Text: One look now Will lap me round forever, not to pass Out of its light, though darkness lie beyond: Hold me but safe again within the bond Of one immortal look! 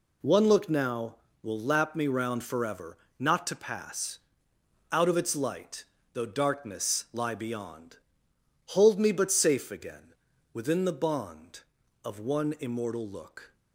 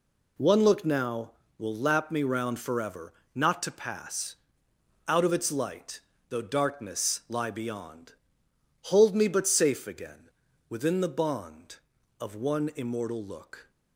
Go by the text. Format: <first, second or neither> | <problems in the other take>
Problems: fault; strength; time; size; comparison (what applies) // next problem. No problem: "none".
neither | pauses between "pass" and "Out"; noticeable; the same in both // pauses between "again" and "within"; the same in both